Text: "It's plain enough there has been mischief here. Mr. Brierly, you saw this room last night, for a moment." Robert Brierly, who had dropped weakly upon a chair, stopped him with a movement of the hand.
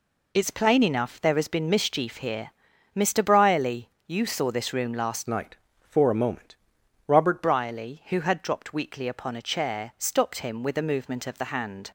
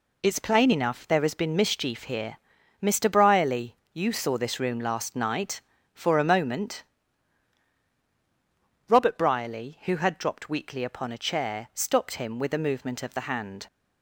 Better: second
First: changes voice from "night" to "Robert"; from 5.2 to 7.4 s; 2.2 s long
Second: none

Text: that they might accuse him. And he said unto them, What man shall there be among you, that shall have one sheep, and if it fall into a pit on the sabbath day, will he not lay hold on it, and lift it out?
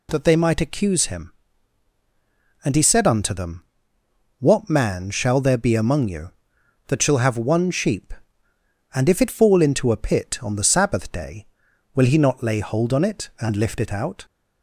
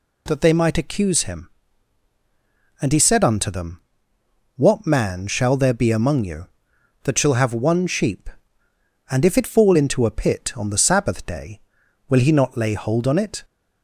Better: first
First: none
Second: stops before "and lift it out"; at 13.4 s

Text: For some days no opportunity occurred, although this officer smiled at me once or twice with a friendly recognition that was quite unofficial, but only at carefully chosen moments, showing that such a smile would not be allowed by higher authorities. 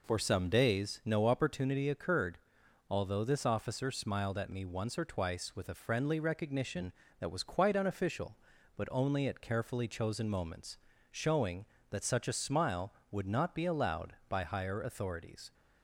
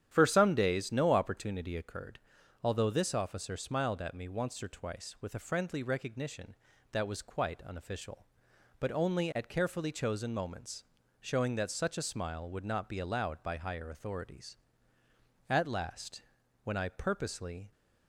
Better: first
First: none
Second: starts louder than the rest; strong; until 1.1 s; 10 dB // goes on to say "At last when I purposely"; strong; from 15.4 s on; 2.2 s long

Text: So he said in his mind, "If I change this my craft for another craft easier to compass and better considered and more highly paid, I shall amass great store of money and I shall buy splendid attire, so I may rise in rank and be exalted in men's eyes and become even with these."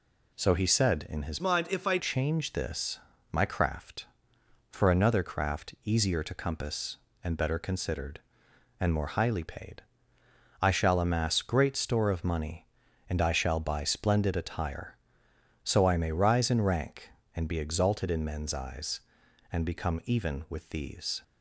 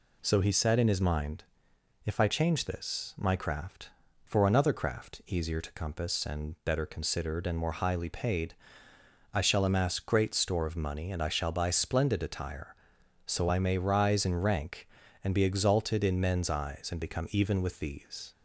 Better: second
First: changes voice from "mind" to "I"; from 1.3 to 1.9 s; 0.6 s long // pauses between "this" and "my"; slight; at 2.9 s; 0.32 s long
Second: none

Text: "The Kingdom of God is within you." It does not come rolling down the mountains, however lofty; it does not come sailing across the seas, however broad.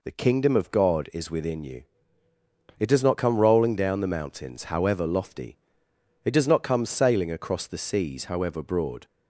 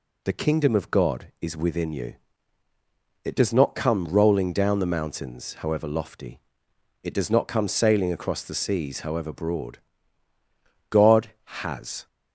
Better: first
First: none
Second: goes on to say "God has"; noticeable; from 10.9 s on; 1.1 s long

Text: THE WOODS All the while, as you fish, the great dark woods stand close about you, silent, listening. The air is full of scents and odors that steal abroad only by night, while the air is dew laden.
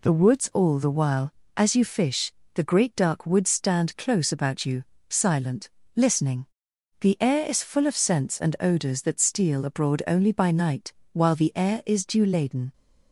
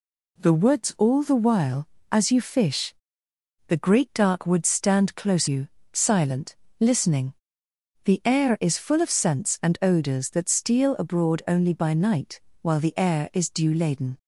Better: first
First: none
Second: skips "about"; at 5.4 s

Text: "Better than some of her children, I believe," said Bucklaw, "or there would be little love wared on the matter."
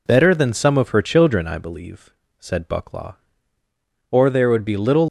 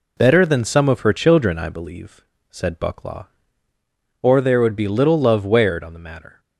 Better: second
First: stops before "love wared on the matter"; at 5.0 s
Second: none

